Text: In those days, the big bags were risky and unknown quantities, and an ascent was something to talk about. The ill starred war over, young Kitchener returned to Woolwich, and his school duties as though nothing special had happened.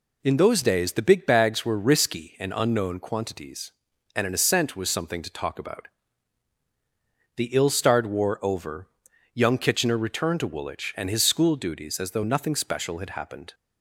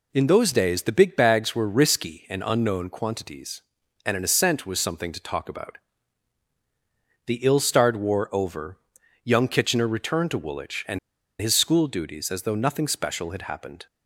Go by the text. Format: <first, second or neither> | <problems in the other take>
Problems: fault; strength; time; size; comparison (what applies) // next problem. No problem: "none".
first | pauses between "and" and "his"; at 10.9 s; 0.41 s long